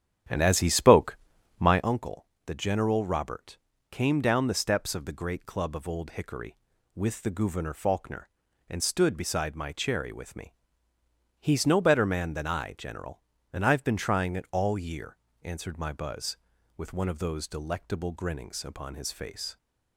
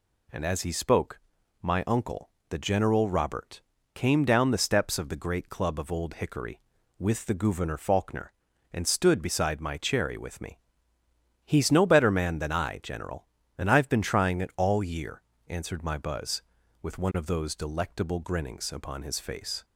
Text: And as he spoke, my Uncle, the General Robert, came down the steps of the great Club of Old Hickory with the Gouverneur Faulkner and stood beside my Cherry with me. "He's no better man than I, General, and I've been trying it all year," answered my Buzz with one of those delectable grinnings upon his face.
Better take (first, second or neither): second